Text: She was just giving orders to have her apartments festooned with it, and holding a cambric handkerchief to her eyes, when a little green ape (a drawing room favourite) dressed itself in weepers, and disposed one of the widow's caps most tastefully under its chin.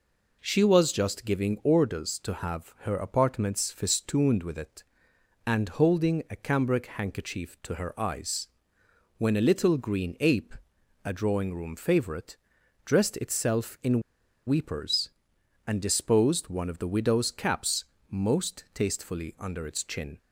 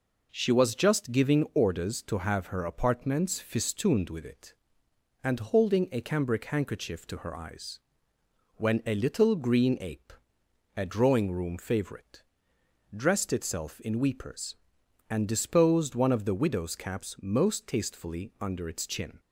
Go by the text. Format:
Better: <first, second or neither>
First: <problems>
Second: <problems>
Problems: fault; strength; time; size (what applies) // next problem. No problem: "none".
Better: second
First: pauses between "in" and "weepers"; noticeable; at 14.0 s; 0.46 s long // pauses between "caps" and "most"; slight; at 17.8 s; 0.24 s long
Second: none